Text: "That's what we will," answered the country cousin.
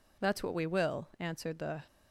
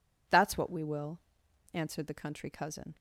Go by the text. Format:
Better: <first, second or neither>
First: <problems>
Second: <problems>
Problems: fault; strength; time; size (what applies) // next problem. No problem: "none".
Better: second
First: stops before "country cousin"; at 1.8 s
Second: none